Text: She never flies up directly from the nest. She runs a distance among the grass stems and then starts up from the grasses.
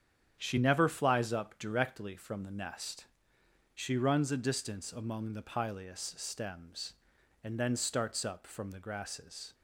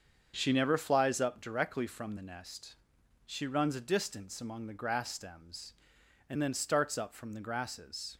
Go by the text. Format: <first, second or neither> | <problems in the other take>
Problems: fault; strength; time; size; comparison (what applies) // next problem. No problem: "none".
second | starts louder than the rest; strong; until 1.3 s; 8.5 dB; also in the second // says "pileus" for "grass"; at 5.4 s